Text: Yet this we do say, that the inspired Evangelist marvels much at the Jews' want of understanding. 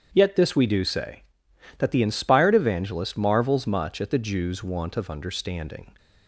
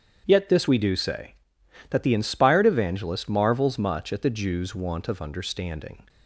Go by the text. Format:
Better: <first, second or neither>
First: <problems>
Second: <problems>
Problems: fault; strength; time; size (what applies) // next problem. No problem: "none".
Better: neither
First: starts louder than the rest; strong; until 1.1 s; 8 dB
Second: starts louder than the rest; strong; until 1.2 s; 8 dB